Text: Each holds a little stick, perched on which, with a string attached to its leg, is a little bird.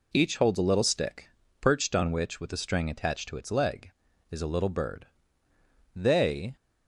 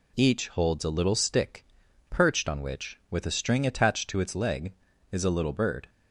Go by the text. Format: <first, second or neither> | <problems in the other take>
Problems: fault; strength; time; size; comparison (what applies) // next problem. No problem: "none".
second | goes on to say "They"; from 5.9 s on; 0.60 s long